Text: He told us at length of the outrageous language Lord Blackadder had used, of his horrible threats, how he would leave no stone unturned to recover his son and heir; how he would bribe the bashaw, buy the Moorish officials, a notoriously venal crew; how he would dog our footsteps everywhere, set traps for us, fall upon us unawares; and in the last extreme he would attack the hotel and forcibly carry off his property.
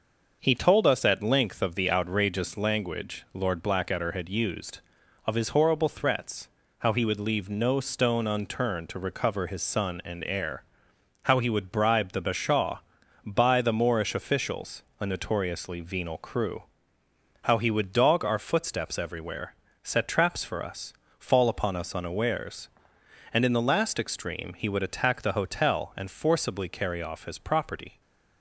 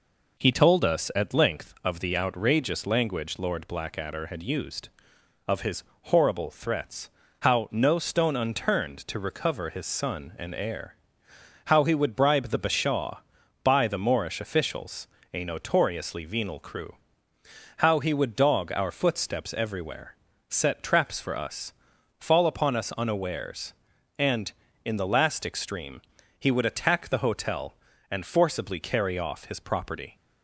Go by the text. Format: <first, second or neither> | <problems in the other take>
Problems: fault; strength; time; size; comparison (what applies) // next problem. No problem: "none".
first | pauses between "his" and "horrible"; slight; at 5.8 s; 0.20 s long // skips "he would leave"; at 7.7 s // pauses between "extreme" and "he"; at 26.0 s; 0.38 s long